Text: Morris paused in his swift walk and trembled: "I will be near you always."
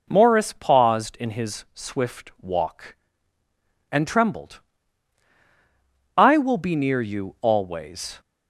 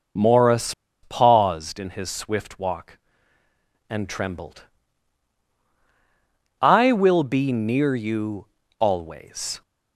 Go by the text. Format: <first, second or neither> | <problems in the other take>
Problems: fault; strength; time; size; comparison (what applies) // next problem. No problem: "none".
first | pauses between "Morris" and "paused"; slight; at 0.7 s; 0.30 s long // pauses between "you" and "always"; slight; at 8.4 s; 0.32 s long